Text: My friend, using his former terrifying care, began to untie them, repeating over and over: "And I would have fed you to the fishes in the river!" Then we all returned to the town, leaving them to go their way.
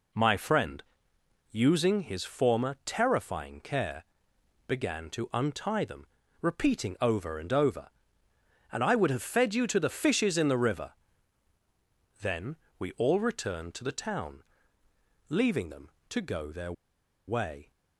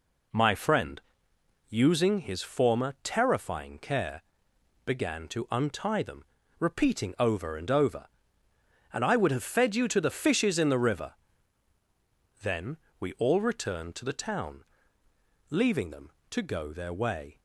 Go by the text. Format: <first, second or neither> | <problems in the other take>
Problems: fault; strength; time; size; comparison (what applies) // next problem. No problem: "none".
second | pauses between "Then" and "we"; slight; at 12.5 s; 0.22 s long; slight in the second // pauses between "their" and "way"; noticeable; at 16.7 s; 0.53 s long